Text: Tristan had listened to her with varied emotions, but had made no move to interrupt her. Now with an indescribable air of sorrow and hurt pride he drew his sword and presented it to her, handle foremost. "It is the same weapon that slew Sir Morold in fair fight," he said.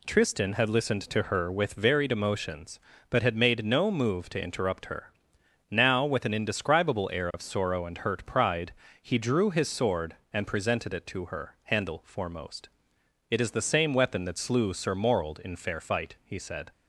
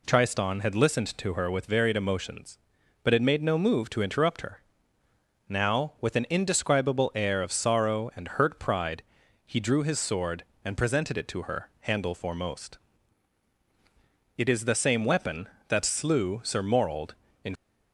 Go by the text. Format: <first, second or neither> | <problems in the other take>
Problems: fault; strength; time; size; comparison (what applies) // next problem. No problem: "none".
first | pauses between "pride" and "he"; at 9.0 s; 0.42 s long; slight in the first // stops before "fair fight he said"; at 17.5 s